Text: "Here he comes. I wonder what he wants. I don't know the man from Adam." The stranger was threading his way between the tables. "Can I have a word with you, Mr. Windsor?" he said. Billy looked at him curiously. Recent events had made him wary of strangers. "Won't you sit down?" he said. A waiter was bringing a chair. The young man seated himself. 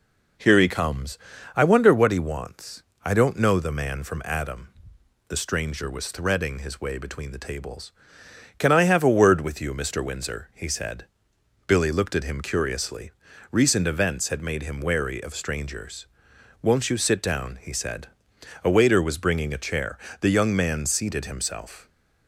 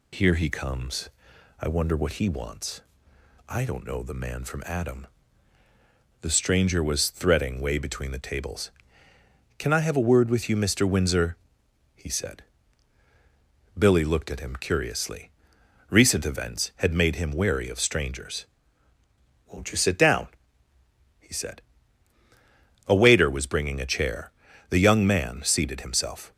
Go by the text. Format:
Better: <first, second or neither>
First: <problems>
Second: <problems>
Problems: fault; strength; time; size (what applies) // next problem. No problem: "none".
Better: first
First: none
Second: skips "his"; at 7.5 s